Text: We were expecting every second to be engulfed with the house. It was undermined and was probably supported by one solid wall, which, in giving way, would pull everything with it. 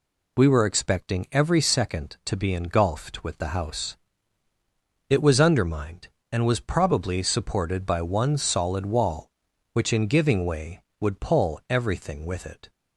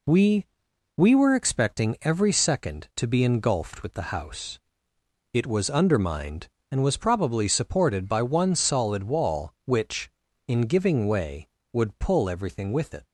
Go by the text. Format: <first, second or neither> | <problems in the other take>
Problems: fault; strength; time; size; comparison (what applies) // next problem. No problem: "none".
first | says "We" twice; at 0.9 s